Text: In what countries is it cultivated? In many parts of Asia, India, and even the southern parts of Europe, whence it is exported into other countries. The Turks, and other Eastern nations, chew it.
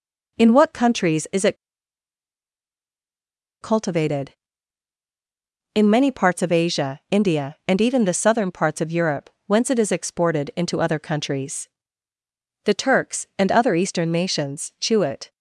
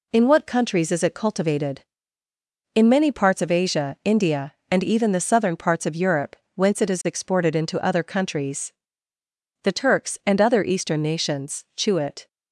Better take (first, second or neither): second